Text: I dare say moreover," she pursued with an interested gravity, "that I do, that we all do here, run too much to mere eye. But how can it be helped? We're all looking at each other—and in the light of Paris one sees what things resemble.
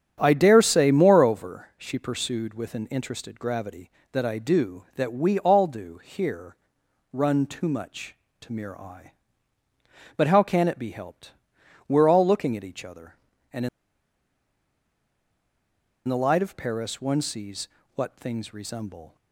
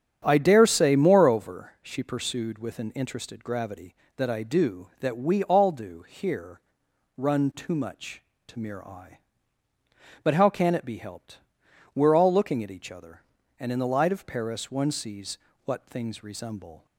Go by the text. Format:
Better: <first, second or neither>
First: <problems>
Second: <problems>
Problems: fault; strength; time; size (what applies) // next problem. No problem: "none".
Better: second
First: starts louder than the rest; strong; until 1.2 s; 8.5 dB // pauses between "in" and "the"; strong; at 13.6 s; 2.3 s long // pauses between "sees" and "what"; slight; at 17.6 s; 0.28 s long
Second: starts louder than the rest; strong; until 1.2 s; 8.5 dB // pauses between "sees" and "what"; slight; at 15.3 s; 0.28 s long